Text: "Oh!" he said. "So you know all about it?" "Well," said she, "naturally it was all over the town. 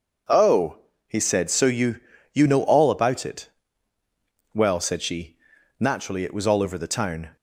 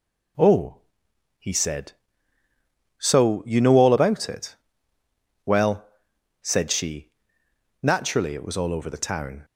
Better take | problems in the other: second | says "you" twice; at 2.3 s

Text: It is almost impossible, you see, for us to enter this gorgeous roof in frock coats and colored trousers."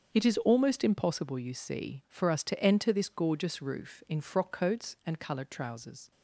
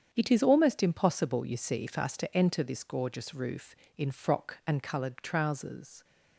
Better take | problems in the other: first | starts louder than the rest; strong; until 1.1 s; 8 dB; also in the first // skips "coats"; at 4.6 s

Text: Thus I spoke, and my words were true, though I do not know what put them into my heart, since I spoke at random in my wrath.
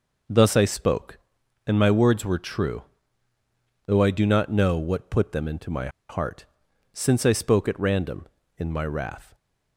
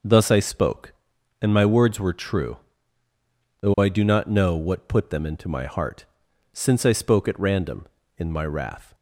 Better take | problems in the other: second | pauses between "my" and "heart"; slight; at 5.8 s; 0.20 s long

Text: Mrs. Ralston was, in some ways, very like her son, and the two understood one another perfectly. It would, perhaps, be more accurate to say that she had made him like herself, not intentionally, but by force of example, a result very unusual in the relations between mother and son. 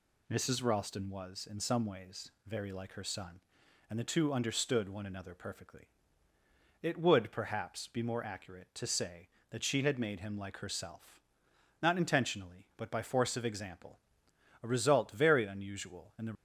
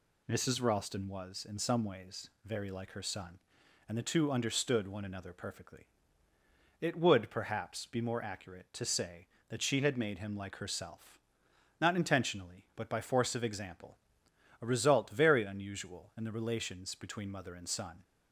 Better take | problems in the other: second | stops before "relations between mother and son"; at 16.3 s

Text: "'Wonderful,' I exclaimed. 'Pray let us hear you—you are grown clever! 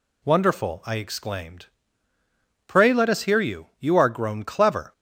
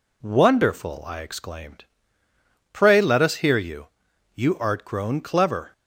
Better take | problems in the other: first | says "art" for "are"; at 4.5 s

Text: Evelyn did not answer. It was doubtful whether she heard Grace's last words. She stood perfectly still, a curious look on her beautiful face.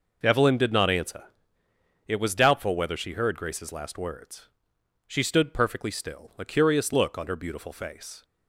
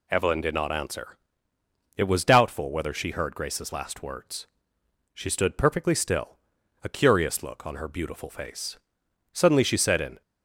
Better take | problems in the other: first | goes on to say "Suddenly she said in"; noticeable; from 9.3 s on; 0.88 s long

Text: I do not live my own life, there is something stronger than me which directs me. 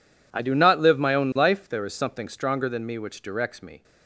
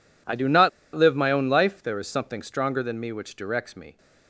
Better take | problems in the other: first | pauses between "not" and "live"; slight; at 0.6 s; 0.25 s long

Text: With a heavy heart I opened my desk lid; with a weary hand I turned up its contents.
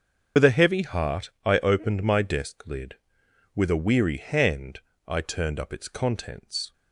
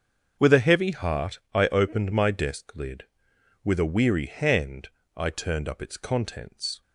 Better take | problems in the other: second | loses the start of "With"; at 0.3 s; 55 ms // starts louder than the rest; until 1.5 s; 7 dB; also in the second // pauses between "heart" and "I"; slight; at 1.2 s; 0.16 s long; slight in the second // pauses between "hand" and "I"; slight; at 4.7 s; 0.28 s long; slight in the second

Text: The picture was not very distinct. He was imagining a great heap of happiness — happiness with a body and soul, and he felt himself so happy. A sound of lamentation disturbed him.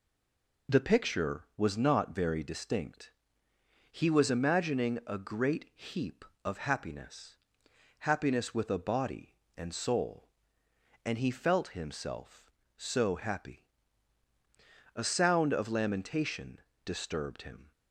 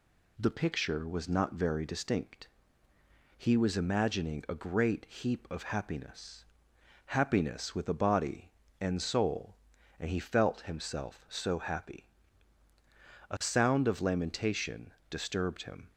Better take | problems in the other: second | stays silent before the first word; slight; until 0.6 s; 0.6 s long // pauses between "lamentation" and "disturbed"; slight; at 16.5 s; 0.26 s long; slight in the second

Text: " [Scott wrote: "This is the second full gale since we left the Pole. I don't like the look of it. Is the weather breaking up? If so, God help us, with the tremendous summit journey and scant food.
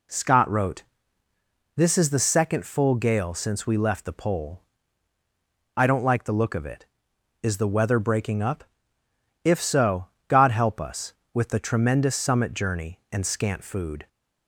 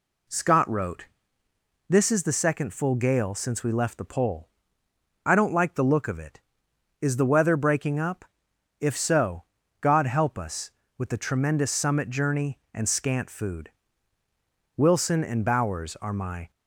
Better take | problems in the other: first | goes on to say "Wilson and Bowers are my"; strong; from 14.7 s on; 1.7 s long

